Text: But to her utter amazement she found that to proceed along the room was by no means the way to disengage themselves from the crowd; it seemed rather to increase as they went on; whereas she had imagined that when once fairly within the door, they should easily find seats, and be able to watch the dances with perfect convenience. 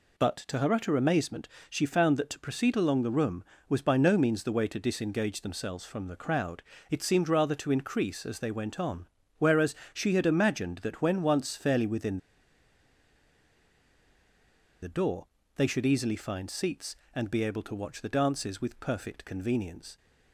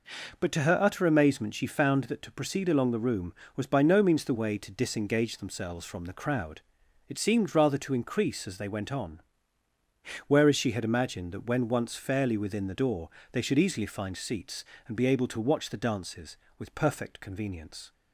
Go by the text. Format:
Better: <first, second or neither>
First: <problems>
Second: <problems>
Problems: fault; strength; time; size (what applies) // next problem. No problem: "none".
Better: second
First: pauses between "amazement" and "she"; slight; at 1.4 s; 0.20 s long // pauses between "whereas" and "she"; slight; at 9.7 s; 0.18 s long // pauses between "within" and "the"; strong; at 12.1 s; 2.6 s long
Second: none